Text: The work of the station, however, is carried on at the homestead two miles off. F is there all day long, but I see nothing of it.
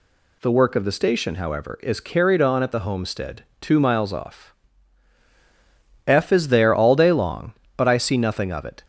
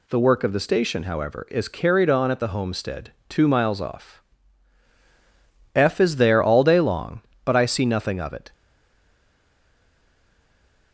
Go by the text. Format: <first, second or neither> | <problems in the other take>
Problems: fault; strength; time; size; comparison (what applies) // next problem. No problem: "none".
first | pauses between "homestead" and "two"; slight; at 3.1 s; 0.18 s long; slight in the first // stays silent after the last word; from 8.5 s on; 2.4 s long